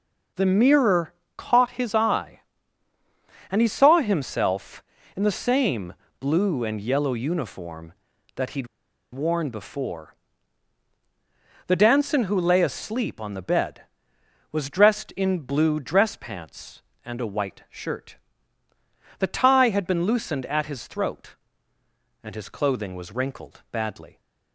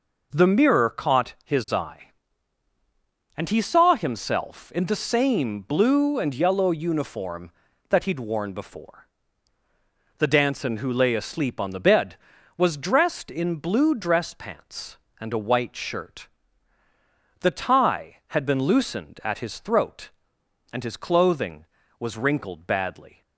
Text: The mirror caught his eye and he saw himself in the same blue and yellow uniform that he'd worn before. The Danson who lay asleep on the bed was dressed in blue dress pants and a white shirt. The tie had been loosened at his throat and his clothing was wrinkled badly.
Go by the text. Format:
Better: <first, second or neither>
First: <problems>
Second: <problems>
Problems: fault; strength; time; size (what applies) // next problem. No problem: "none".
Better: second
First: pauses between "mirror" and "caught"; slight; at 1.1 s; 0.24 s long // pauses between "same" and "blue"; slight; at 5.9 s; 0.26 s long // pauses between "he'd" and "worn"; at 8.6 s; 0.45 s long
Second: none